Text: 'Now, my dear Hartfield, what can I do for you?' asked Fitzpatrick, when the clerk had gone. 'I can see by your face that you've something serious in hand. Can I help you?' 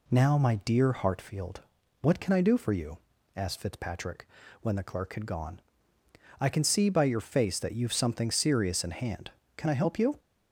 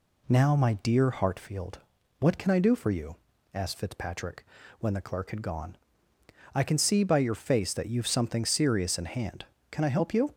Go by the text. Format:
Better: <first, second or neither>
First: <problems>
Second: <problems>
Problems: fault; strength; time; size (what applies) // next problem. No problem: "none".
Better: neither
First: none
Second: none